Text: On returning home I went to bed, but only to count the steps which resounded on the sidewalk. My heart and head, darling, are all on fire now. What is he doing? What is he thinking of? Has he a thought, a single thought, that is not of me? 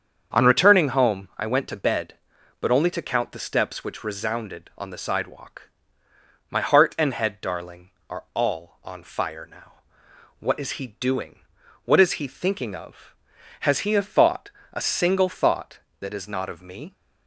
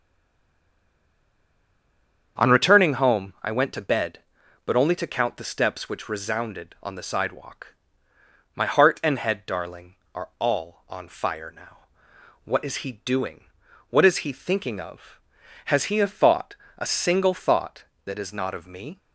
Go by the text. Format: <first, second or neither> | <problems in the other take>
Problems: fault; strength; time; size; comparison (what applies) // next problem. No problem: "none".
first | stays silent before the first word; until 2.3 s; 2.3 s long // starts louder than the rest; strong; until 3.4 s; 7.5 dB; strong in the first